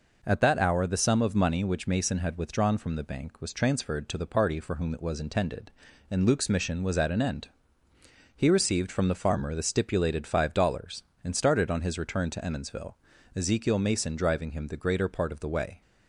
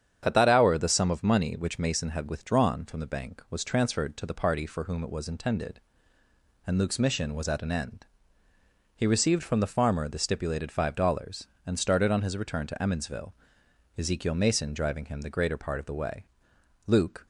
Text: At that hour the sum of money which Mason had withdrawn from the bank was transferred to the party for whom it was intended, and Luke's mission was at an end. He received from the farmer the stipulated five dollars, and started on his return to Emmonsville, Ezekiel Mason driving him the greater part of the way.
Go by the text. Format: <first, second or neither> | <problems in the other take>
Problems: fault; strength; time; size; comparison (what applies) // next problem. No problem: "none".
first | starts louder than the rest; strong; until 1.2 s; 8.5 dB // goes on to say "Luke"; slight; from 16.8 s on; 0.40 s long